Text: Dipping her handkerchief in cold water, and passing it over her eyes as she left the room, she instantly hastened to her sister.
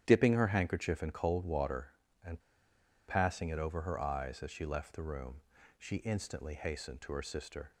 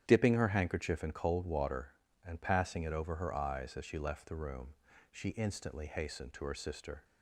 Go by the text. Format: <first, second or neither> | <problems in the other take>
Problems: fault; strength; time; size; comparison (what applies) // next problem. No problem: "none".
second | starts louder than the rest; strong; until 1.0 s; 10 dB; strong in the second // pauses between "and" and "passing"; noticeable; at 2.3 s; 0.68 s long